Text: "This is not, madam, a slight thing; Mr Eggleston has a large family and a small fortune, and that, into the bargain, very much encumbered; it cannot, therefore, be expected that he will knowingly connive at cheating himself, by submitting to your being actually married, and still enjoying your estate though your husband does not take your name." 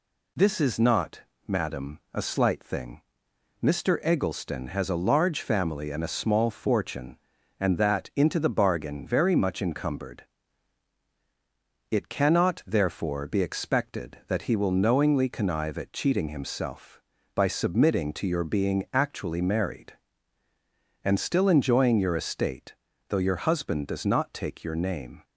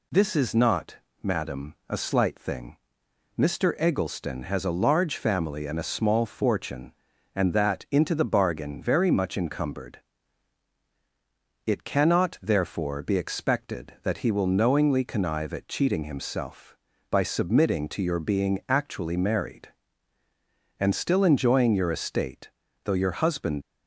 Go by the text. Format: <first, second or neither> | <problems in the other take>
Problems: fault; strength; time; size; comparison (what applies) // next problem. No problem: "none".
first | pauses between "estate" and "though"; slight; at 22.5 s; 0.32 s long; slight in the first // stops before "does not take your name"; at 23.6 s